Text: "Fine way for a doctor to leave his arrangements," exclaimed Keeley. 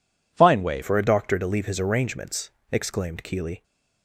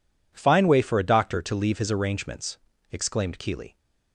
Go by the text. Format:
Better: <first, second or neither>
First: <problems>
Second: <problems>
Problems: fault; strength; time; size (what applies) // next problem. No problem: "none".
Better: second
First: changes voice at "for"; from 0.8 s on; 2.8 s long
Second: none